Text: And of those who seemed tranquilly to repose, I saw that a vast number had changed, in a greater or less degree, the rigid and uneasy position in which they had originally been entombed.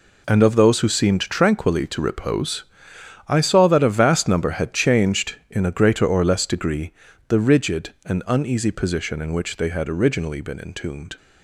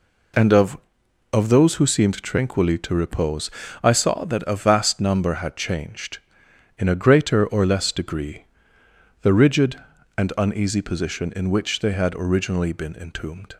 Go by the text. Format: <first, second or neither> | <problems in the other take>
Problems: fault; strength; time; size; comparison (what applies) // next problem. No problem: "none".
first | says "of" twice; at 1.3 s